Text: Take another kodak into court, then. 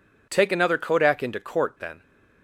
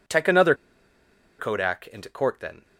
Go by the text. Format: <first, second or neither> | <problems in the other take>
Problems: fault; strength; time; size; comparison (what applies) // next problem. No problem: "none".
first | pauses between "another" and "kodak"; noticeable; at 0.5 s; 0.84 s long